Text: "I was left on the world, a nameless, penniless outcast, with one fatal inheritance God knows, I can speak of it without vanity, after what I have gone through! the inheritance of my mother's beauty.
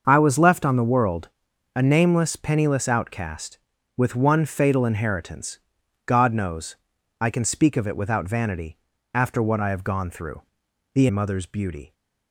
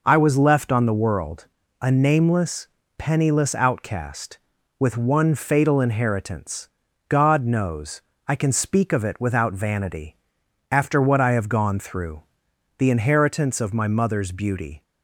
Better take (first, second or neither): second